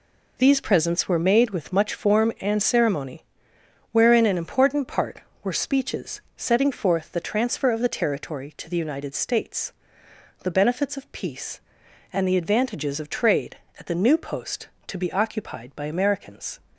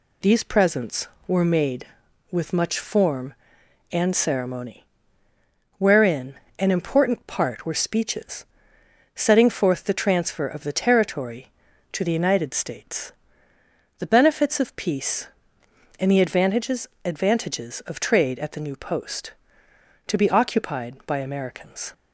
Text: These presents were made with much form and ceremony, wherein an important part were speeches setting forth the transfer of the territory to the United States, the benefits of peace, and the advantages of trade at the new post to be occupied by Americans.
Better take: first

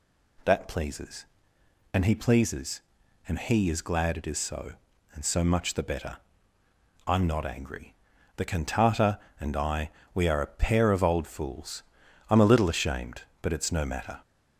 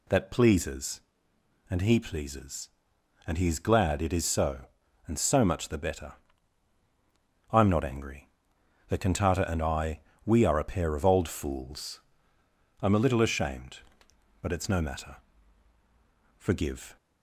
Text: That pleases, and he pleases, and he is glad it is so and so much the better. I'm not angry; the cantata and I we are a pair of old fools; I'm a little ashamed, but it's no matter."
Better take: first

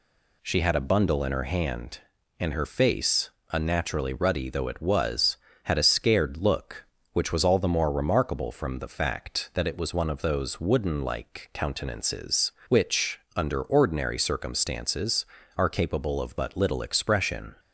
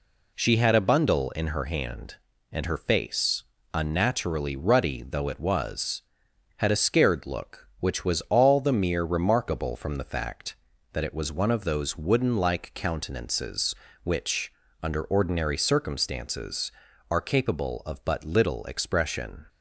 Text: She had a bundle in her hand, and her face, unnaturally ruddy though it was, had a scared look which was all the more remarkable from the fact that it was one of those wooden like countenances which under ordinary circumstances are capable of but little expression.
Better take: first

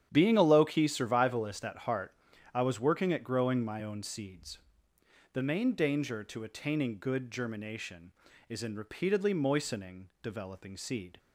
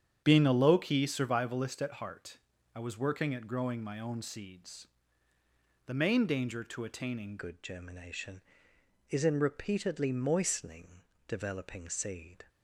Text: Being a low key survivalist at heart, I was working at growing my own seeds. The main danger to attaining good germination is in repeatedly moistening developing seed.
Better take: first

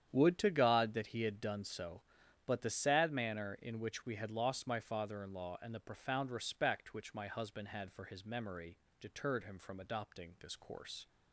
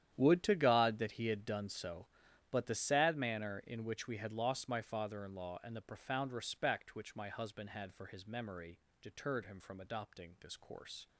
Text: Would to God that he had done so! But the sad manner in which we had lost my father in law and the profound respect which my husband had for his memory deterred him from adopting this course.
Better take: first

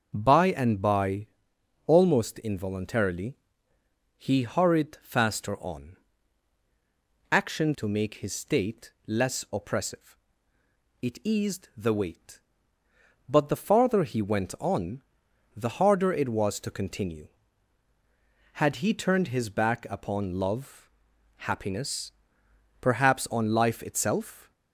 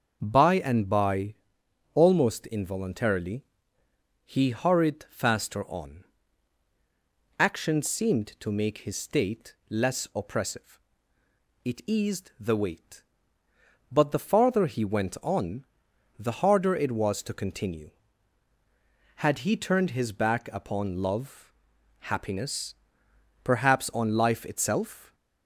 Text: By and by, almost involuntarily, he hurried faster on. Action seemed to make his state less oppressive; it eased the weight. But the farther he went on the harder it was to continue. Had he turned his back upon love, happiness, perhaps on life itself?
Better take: second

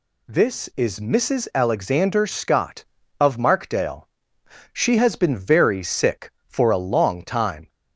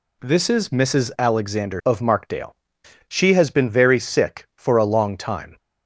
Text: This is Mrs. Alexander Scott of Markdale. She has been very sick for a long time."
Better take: first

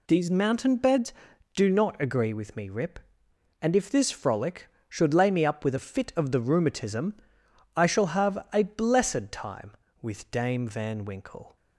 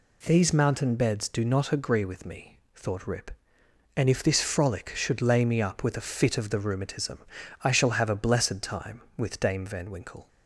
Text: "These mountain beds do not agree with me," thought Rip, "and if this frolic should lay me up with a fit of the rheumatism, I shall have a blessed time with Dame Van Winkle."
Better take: second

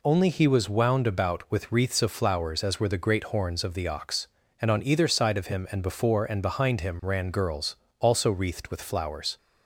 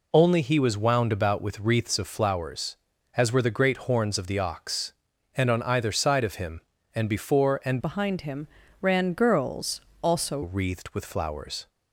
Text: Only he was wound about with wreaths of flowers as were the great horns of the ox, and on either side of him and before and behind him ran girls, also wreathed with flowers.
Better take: first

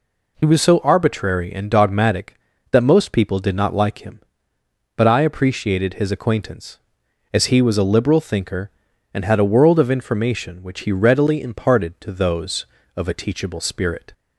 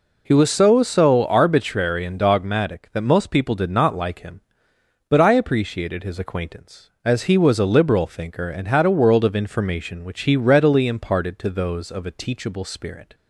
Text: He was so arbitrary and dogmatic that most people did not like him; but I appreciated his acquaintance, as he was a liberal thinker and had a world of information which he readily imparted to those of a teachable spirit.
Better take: first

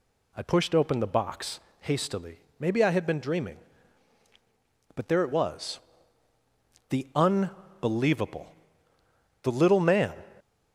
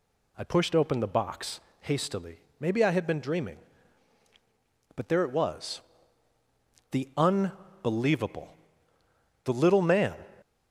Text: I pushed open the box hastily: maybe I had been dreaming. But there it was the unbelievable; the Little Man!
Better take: neither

